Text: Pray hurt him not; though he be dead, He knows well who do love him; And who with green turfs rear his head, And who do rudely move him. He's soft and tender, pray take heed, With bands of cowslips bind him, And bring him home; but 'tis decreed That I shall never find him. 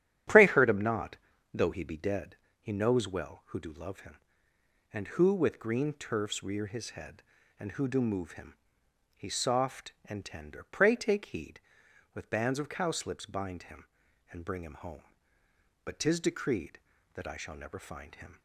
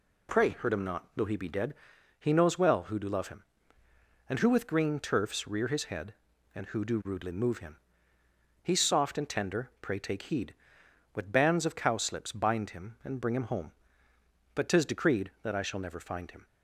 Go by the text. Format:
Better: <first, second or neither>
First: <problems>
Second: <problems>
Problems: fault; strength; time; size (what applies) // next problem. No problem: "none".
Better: second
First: starts louder than the rest; strong; until 1.7 s; 10.5 dB // skips "rudely"; at 8.0 s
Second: none